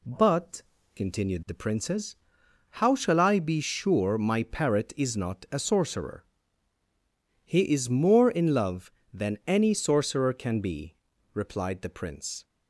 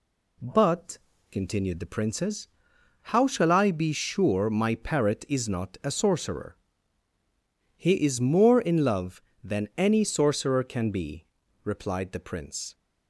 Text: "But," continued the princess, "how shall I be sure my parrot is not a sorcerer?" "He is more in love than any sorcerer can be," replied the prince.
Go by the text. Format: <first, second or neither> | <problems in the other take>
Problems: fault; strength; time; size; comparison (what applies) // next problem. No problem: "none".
neither | none